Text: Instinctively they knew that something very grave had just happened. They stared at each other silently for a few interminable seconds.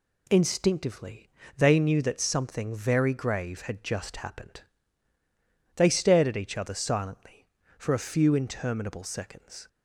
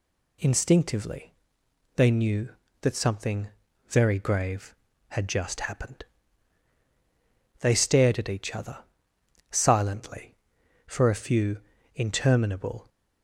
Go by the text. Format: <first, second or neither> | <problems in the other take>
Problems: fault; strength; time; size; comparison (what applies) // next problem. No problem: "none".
first | pauses between "Instinctively" and "they"; noticeable; at 1.3 s; 0.64 s long; slight in the first // pauses between "something" and "very"; at 3.4 s; 0.40 s long // pauses between "other" and "silently"; noticeable; at 8.7 s; 0.72 s long // pauses between "few" and "interminable"; at 11.5 s; 0.38 s long // stops before "seconds"; at 12.8 s